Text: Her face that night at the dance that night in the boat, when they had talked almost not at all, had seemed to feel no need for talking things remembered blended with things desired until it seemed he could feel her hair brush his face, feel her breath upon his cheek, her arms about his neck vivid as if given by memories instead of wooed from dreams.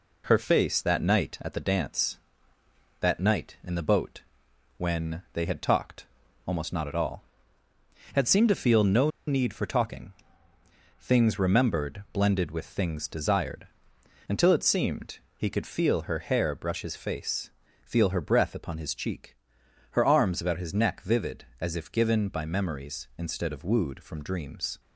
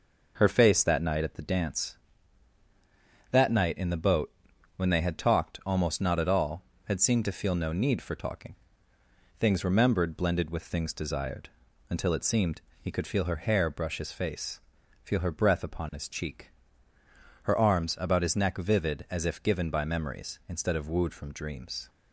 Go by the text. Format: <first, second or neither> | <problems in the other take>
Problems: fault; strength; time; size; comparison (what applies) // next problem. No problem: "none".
second | pauses between "talked" and "almost"; at 6.0 s; 0.40 s long // pauses between "no" and "need"; slight; at 9.1 s; 0.17 s long // pauses between "talking" and "things"; noticeable; at 10.1 s; 0.86 s long; noticeable in the second // pauses between "desired" and "until"; noticeable; at 13.6 s; 0.60 s long; also in the second // pauses between "seemed" and "he"; slight; at 15.1 s; 0.18 s long; slight in the second